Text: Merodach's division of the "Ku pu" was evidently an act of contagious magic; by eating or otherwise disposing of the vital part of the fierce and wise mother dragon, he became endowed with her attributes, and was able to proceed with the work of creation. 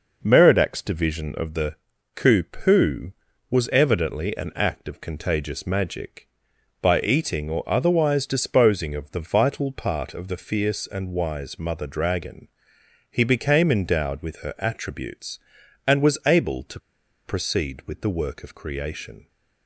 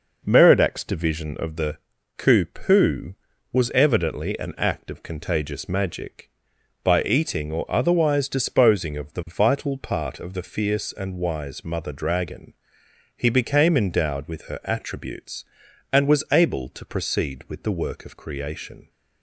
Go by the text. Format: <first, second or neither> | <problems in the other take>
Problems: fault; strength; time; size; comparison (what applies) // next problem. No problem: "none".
second | pauses between "the" and "Ku"; at 1.7 s; 0.38 s long; also in the second // pauses between "to" and "proceed"; noticeable; at 16.7 s; 0.46 s long